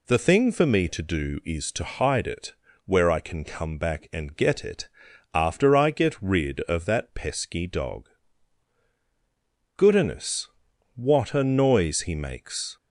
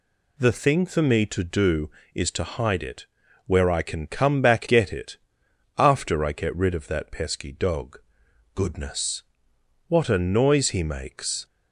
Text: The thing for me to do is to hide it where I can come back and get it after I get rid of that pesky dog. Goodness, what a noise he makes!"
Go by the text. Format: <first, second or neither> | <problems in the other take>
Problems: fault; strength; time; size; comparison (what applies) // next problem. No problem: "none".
first | pauses between "it" and "where"; at 3.0 s; 0.40 s long; slight in the first // skips "and"; at 4.6 s // pauses between "it" and "after"; noticeable; at 5.1 s; 0.60 s long; noticeable in the first